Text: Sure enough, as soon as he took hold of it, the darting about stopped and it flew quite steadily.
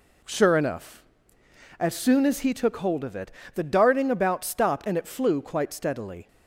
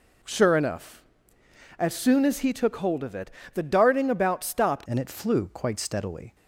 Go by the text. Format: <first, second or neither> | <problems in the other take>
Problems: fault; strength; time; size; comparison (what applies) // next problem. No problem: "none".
first | changes voice at "and"; from 4.8 s on; 1.5 s long